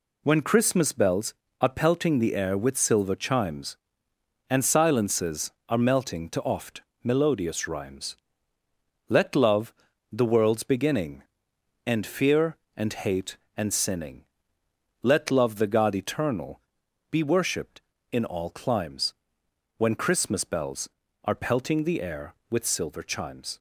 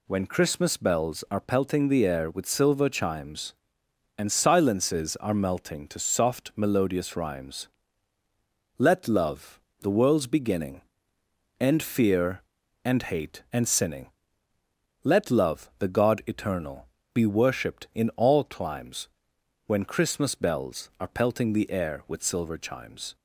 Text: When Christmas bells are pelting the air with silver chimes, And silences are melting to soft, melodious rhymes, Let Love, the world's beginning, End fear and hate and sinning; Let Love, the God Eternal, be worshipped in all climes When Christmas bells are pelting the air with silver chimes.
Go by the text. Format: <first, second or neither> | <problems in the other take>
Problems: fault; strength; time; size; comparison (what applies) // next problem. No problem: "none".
second | says "oft" for "soft"; at 6.4 s // pauses between "climes" and "When"; noticeable; at 19.1 s; 0.64 s long; noticeable in the second